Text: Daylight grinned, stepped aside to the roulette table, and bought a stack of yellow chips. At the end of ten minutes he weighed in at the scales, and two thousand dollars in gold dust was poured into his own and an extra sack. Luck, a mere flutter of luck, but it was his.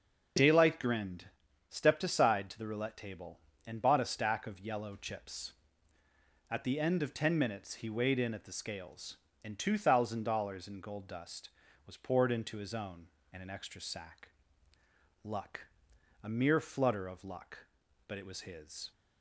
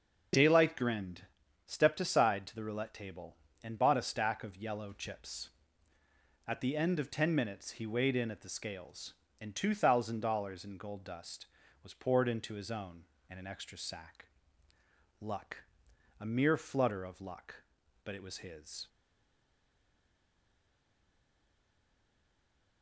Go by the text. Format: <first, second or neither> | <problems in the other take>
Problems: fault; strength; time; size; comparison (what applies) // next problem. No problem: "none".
first | starts louder than the rest; until 1.7 s; 6.5 dB; also in the first // stays silent after the last word; strong; from 18.8 s on; 4.0 s long